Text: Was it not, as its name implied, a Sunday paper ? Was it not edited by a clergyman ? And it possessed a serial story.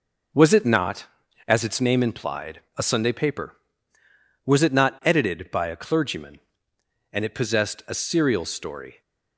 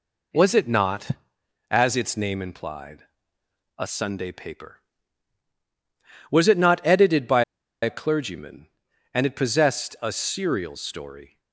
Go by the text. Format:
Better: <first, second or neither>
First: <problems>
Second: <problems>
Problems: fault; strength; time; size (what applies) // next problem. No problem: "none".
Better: first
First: none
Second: pauses between "by" and "a"; at 7.4 s; 0.40 s long